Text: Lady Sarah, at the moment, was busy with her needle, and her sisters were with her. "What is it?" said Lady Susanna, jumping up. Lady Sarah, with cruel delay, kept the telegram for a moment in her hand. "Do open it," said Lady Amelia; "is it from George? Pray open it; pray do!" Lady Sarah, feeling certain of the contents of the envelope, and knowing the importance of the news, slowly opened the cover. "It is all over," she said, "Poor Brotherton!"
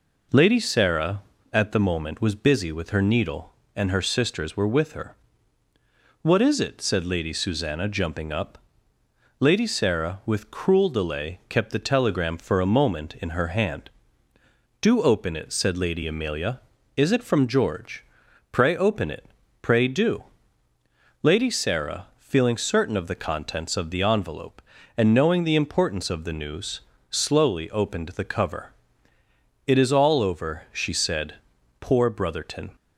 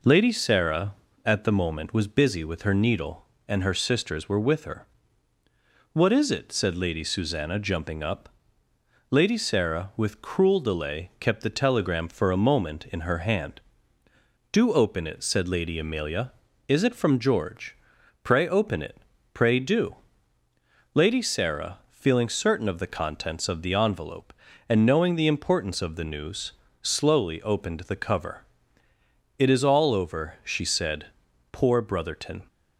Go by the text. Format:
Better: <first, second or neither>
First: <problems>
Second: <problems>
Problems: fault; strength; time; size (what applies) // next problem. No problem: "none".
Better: neither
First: none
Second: none